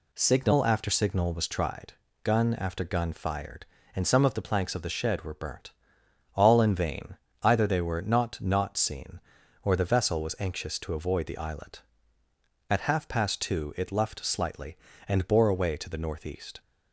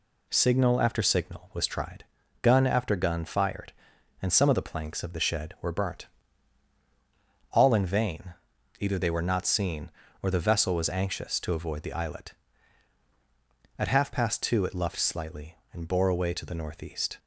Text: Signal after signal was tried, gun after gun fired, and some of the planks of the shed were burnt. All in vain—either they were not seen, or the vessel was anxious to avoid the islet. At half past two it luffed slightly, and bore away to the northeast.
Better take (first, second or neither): second